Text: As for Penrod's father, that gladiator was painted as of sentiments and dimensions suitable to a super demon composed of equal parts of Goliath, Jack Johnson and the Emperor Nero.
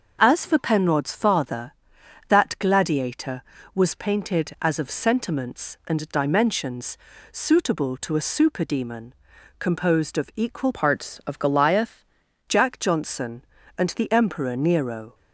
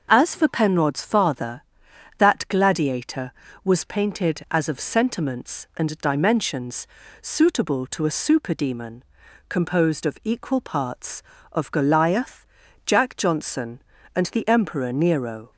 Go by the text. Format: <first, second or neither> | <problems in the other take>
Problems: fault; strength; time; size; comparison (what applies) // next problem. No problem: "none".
second | pauses between "dimensions" and "suitable"; slight; at 6.9 s; 0.34 s long; slight in the second // pauses between "demon" and "composed"; noticeable; at 9.1 s; 0.46 s long; noticeable in the second // changes voice from "parts" to "Goliath"; from 10.7 to 12.0 s; 1.3 s long